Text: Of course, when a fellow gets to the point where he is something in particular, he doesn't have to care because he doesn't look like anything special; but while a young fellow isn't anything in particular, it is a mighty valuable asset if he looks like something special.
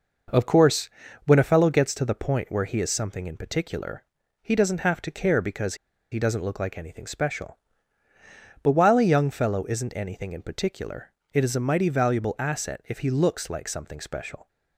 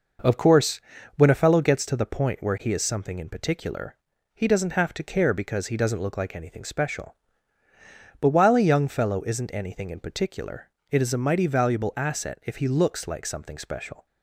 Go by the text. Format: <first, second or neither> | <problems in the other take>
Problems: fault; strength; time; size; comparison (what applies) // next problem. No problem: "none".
second | pauses between "because" and "he"; at 5.7 s; 0.36 s long